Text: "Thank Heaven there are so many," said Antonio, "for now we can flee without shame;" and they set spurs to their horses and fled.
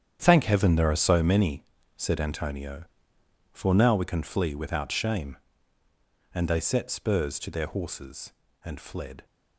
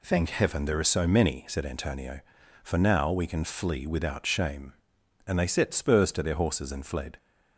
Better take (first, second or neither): second